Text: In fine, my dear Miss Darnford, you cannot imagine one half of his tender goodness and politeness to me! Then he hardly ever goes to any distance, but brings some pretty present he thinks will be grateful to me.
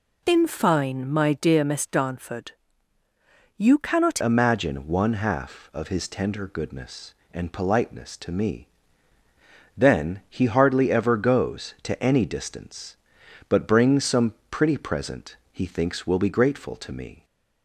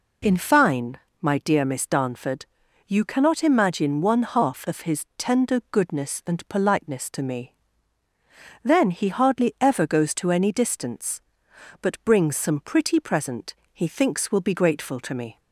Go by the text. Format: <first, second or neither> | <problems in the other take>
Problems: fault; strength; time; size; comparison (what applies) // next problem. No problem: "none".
second | changes voice at "imagine"; from 4.2 s on; 13.0 s long // pauses between "some" and "pretty"; slight; at 14.3 s; 0.16 s long // pauses between "present" and "he"; slight; at 15.3 s; 0.16 s long; slight in the second